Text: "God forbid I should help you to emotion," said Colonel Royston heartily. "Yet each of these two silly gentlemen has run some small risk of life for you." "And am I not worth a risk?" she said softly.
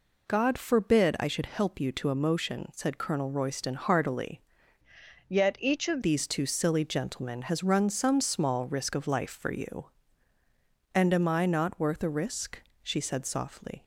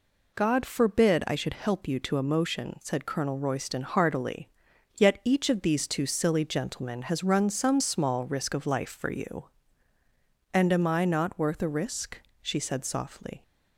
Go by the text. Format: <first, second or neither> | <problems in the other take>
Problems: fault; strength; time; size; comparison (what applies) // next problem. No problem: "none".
second | changes voice from "Yet" to "of"; from 5.2 to 6.0 s; 0.8 s long